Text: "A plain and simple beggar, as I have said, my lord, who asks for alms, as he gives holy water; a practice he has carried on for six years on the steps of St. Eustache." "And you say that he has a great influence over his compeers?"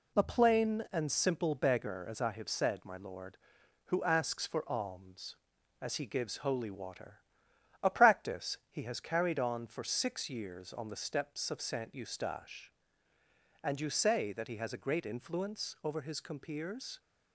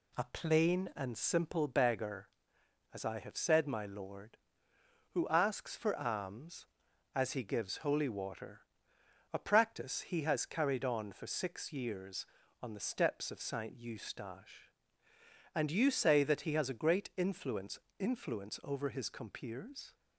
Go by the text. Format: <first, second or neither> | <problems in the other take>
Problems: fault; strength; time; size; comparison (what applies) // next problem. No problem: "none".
first | says "influence" twice; at 17.9 s